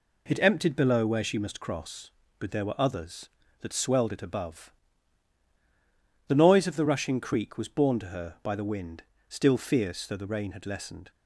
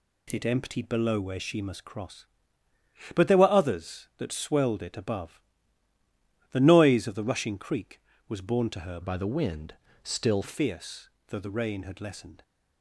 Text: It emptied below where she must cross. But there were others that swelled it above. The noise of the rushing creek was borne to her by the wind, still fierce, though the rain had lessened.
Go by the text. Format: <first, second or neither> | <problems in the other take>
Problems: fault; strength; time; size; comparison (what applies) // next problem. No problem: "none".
first | changes voice from "by" to "still"; from 9.0 to 10.4 s; 1.4 s long